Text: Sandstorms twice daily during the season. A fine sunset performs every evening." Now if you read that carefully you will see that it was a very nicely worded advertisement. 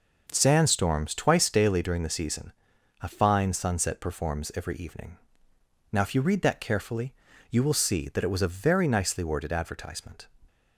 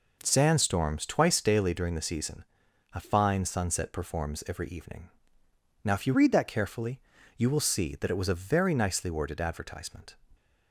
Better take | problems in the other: first | changes voice from "read" to "that"; from 6.1 to 6.4 s; 0.3 s long // pauses between "carefully" and "you"; at 6.9 s; 0.38 s long; also in the first

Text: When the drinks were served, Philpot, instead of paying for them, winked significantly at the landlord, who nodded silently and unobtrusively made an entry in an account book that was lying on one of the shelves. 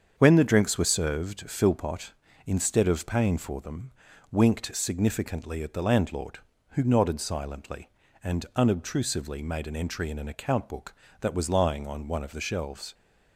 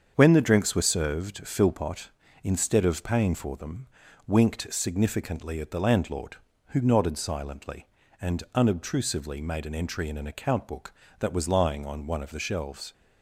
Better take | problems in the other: neither | starts louder than the rest; strong; the same in both

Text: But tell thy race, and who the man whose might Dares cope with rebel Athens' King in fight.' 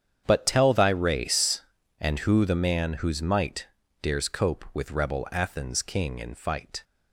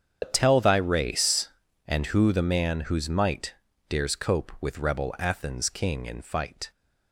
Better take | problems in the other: first | loses the start of "But"; at 0.2 s; 95 ms // starts louder than the rest; strong; until 1.2 s; 7.5 dB; strong in the first // pauses between "might" and "Dares"; slight; at 3.5 s; 0.36 s long; slight in the first

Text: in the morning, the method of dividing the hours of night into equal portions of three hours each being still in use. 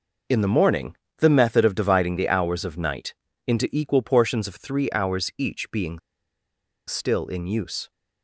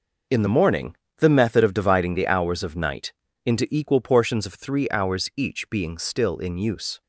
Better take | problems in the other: second | pauses between "night" and "into"; slight; at 3.1 s; 0.32 s long; slight in the second // pauses between "being" and "still"; noticeable; at 5.9 s; 0.88 s long

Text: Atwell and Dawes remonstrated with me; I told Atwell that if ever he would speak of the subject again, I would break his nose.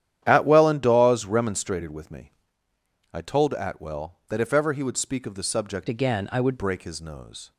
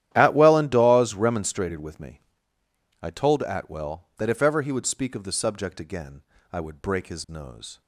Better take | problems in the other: second | starts louder than the rest; strong; until 1.2 s; 11 dB; strong in the second // changes voice from "again" to "would"; from 5.8 to 6.5 s; 0.7 s long

